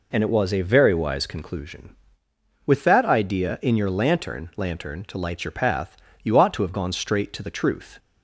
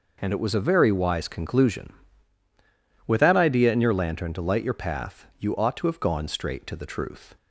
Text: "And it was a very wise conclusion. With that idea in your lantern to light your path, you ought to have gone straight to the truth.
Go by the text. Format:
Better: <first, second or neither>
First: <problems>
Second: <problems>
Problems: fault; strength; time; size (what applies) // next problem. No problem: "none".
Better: second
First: says "lantern" twice; at 4.5 s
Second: none